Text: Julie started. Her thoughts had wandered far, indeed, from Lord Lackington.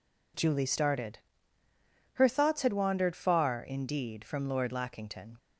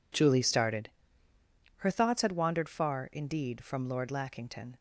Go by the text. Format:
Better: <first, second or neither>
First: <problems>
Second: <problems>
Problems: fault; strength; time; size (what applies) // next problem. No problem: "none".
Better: neither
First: none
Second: none